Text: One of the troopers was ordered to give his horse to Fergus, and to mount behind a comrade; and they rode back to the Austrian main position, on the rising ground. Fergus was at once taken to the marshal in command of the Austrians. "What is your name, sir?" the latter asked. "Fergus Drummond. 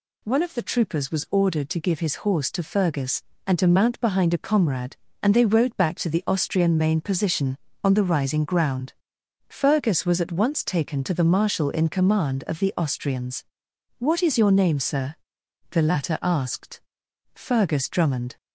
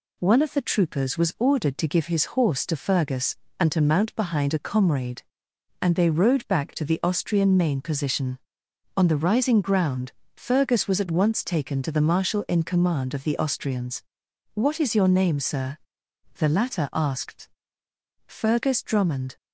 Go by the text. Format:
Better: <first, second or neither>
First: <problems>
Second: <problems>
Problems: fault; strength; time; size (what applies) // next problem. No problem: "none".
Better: neither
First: none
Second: none